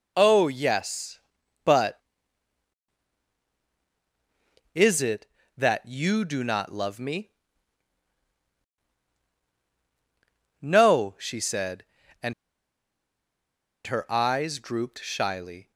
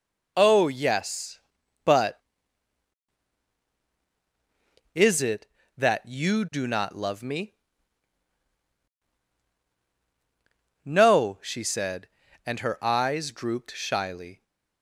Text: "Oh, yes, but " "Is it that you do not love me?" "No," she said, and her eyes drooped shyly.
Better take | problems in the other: second | pauses between "and" and "her"; strong; at 12.3 s; 1.5 s long

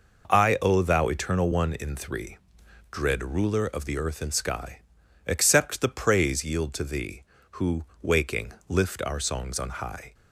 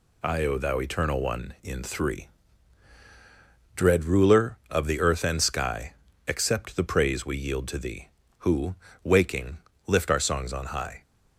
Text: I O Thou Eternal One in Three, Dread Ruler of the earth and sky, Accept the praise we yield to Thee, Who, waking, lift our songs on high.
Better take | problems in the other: second | skips "we"; at 6.4 s

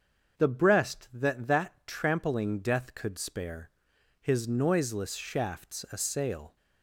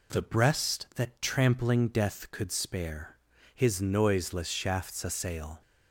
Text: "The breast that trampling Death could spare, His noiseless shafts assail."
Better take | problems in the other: second | starts louder than the rest; until 1.4 s; 7 dB // says "that" twice; at 1.4 s

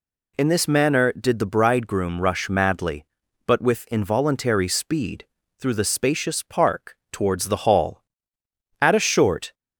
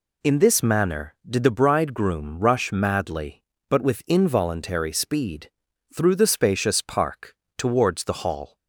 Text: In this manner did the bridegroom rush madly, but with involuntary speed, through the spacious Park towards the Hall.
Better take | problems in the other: second | pauses between "Park" and "towards"; slight; at 6.9 s; 0.16 s long; slight in the second // goes on to say "At a short"; noticeable; from 8.8 s on; 0.72 s long

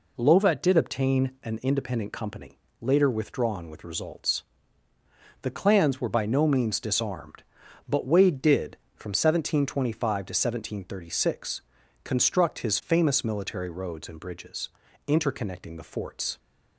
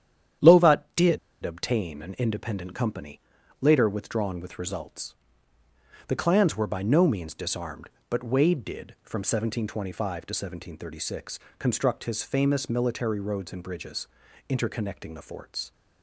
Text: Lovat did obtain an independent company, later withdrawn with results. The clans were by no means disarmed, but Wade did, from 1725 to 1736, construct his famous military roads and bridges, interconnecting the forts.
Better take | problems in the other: first | starts louder than the rest; strong; until 1.7 s; 10 dB // pauses between "did" and "obtain"; slight; at 1.1 s; 0.25 s long

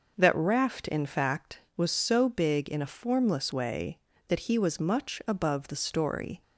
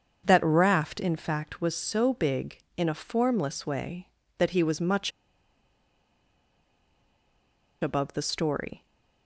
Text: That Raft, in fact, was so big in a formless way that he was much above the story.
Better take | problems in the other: first | starts louder than the rest; until 1.2 s; 7 dB // pauses between "much" and "above"; strong; at 5.1 s; 2.7 s long

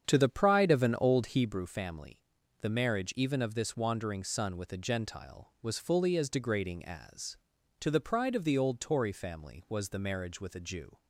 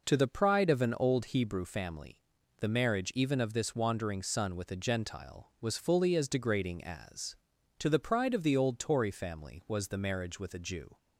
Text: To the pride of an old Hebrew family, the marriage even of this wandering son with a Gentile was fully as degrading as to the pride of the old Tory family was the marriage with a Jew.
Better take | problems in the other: second | starts louder than the rest; strong; until 1.5 s; 8 dB

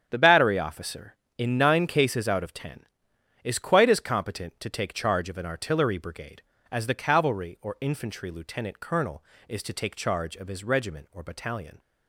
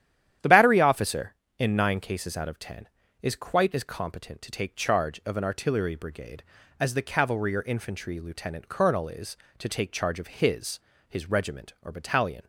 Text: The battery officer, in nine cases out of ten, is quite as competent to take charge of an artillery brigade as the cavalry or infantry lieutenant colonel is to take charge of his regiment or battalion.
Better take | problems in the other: first | starts louder than the rest; strong; until 1.6 s; 10.5 dB; strong in the first // says "his" twice; at 11.0 s

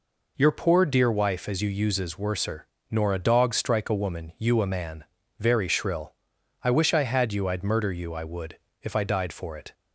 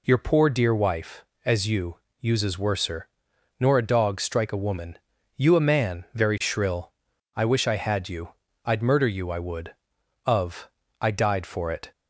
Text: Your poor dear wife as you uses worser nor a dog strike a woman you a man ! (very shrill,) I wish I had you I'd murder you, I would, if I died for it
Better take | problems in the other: first | pauses between "you" and "uses"; slight; at 1.9 s; 0.26 s long // pauses between "worser" and "nor"; noticeable; at 3.0 s; 0.52 s long; slight in the first // pauses between "woman" and "you"; slight; at 4.9 s; 0.36 s long // pauses between "you" and "I'd"; slight; at 8.2 s; 0.34 s long // says "of" for "if"; at 10.2 s

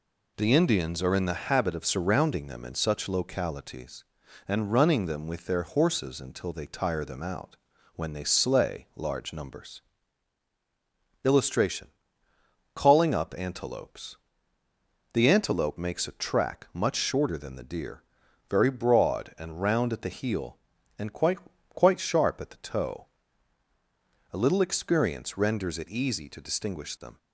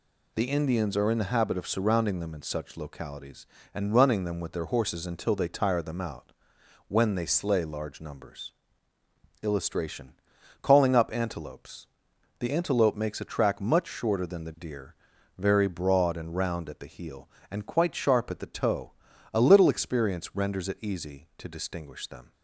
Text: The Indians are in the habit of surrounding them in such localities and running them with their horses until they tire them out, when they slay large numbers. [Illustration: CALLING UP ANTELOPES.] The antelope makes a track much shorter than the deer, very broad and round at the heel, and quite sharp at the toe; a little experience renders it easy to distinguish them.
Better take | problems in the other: second | says "quite" twice; at 21.6 s

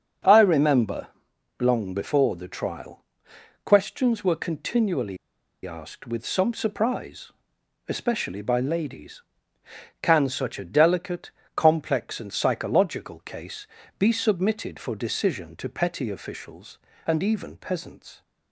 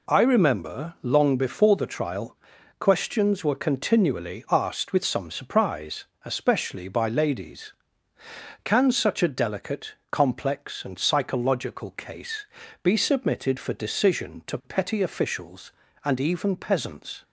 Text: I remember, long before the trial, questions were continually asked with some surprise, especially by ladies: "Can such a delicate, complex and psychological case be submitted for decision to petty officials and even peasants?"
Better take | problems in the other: second | starts louder than the rest; until 1.7 s; 7 dB // pauses between "continually" and "asked"; noticeable; at 5.1 s; 0.48 s long // pauses between "case" and "be"; slight; at 13.6 s; 0.32 s long; also in the second

